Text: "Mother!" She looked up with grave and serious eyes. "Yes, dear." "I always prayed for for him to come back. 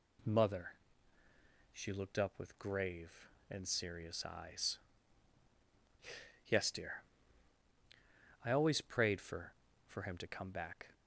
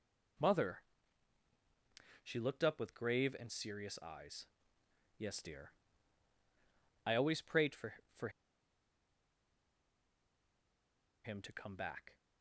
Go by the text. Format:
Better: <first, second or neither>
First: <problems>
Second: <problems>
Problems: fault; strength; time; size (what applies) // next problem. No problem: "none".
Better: first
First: none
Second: pauses between "for" and "him"; strong; at 8.2 s; 2.9 s long